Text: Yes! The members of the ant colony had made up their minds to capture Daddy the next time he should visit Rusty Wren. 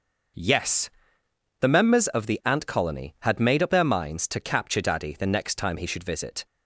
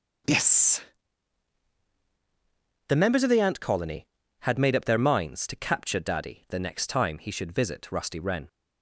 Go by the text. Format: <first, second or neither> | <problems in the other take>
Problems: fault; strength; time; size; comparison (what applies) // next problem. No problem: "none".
second | starts louder than the rest; noticeable; until 2.0 s; 6 dB // stops before "Rusty Wren"; at 6.4 s